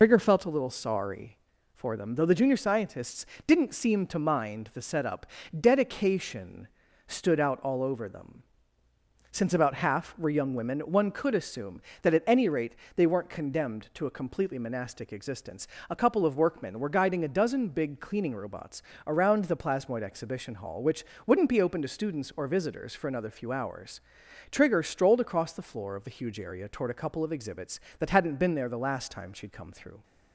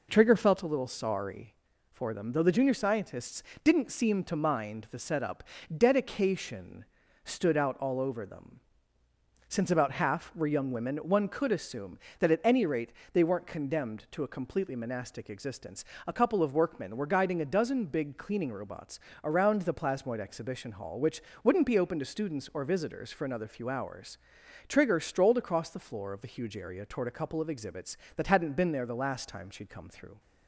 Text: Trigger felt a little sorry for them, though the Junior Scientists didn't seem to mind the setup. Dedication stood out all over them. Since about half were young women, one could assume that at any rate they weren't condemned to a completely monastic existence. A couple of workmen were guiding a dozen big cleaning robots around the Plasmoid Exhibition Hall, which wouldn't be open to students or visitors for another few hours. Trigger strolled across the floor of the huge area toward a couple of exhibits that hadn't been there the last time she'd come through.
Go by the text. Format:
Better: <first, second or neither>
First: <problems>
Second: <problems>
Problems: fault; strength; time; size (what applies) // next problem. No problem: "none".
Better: second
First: loses the start of "Trigger"; at 0.0 s; 95 ms // pauses between "Scientists" and "didn't"; slight; at 3.2 s; 0.20 s long // pauses between "Dedication" and "stood"; at 6.6 s; 0.40 s long // pauses between "rate" and "they"; slight; at 12.7 s; 0.22 s long // pauses between "robots" and "around"; slight; at 18.8 s; 0.24 s long // pauses between "which" and "wouldn't"; slight; at 21.0 s; 0.22 s long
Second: pauses between "Scientists" and "didn't"; slight; at 3.4 s; 0.20 s long // pauses between "Dedication" and "stood"; at 6.8 s; 0.40 s long // pauses between "rate" and "they"; slight; at 12.9 s; 0.22 s long // pauses between "robots" and "around"; slight; at 18.9 s; 0.24 s long // pauses between "which" and "wouldn't"; slight; at 21.1 s; 0.22 s long